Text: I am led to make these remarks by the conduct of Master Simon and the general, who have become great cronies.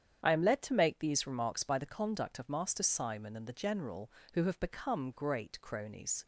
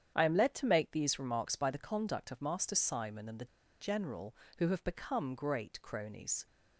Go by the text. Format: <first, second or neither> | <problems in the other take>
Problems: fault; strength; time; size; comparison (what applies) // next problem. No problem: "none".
first | starts louder than the rest; strong; until 1.1 s; 9 dB; strong in the first // pauses between "the" and "general"; slight; at 3.4 s; 0.35 s long